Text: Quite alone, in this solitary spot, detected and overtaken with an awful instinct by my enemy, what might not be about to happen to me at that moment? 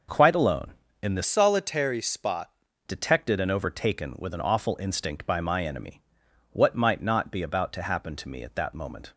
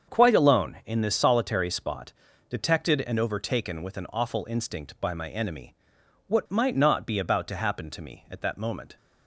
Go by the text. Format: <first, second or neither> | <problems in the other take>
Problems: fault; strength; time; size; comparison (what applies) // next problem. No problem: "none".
second | starts louder than the rest; noticeable; until 1.4 s; 6 dB; also in the second // changes voice from "solitary" to "spot"; from 1.2 to 2.4 s; 1.2 s long